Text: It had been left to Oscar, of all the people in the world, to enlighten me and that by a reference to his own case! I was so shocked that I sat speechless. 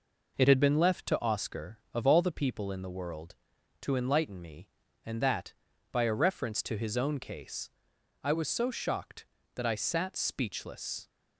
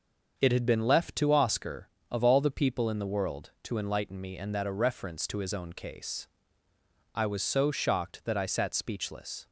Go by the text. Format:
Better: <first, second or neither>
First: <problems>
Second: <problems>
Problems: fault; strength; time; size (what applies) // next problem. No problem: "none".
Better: first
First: none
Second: starts louder than the rest; until 1.3 s; 6 dB // skips "by"; at 4.6 s